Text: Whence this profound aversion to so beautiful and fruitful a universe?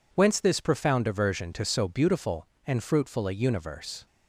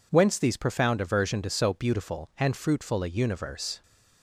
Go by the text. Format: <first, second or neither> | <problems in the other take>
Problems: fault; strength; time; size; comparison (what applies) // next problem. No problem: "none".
first | says "these" for "this"; at 0.3 s